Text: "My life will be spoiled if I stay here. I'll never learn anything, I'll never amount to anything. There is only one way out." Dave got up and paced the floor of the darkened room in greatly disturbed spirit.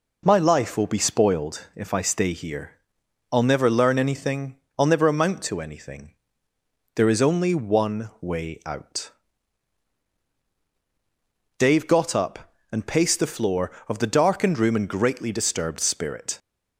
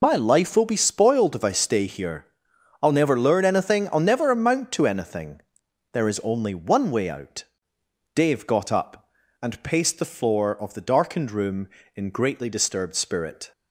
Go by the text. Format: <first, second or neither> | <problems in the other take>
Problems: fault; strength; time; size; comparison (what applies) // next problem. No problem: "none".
first | loses the start of "My"; at 0.0 s; 45 ms